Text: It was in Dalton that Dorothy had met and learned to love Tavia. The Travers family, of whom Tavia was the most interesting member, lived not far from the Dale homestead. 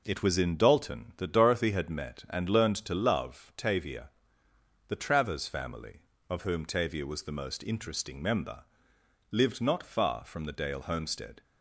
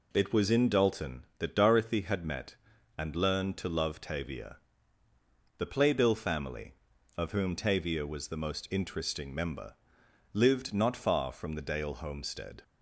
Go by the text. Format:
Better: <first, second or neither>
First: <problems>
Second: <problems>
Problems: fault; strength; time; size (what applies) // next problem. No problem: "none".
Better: first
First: none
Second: says "Playbill" for "Travers"; at 5.6 s